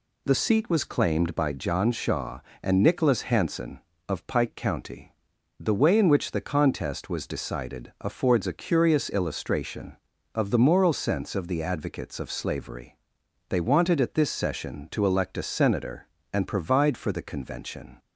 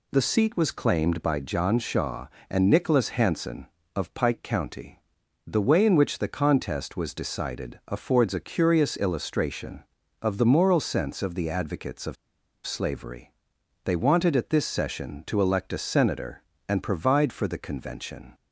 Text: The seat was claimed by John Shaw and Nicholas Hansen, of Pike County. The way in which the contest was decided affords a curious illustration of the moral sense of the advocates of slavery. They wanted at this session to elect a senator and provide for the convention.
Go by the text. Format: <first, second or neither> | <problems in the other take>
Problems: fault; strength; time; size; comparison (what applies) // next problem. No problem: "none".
first | pauses between "of" and "slavery"; noticeable; at 12.1 s; 0.51 s long